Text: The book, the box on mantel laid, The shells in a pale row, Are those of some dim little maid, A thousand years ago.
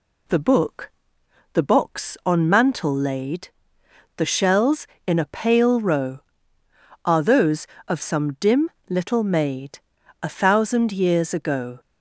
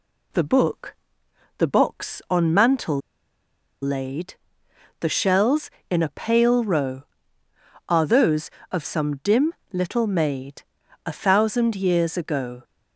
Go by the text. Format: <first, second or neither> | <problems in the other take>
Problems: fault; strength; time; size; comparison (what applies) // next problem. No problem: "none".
first | pauses between "mantel" and "laid"; noticeable; at 2.9 s; 0.83 s long // pauses between "dim" and "little"; slight; at 9.5 s; 0.20 s long; slight in the first